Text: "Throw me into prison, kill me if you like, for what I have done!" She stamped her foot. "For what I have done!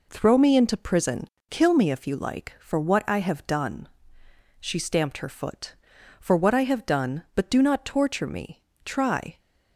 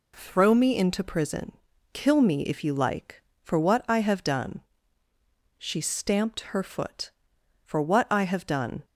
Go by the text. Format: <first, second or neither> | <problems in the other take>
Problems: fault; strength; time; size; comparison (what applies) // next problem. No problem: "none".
second | goes on to say "But do not torture me try"; strong; from 7.3 s on; 2.0 s long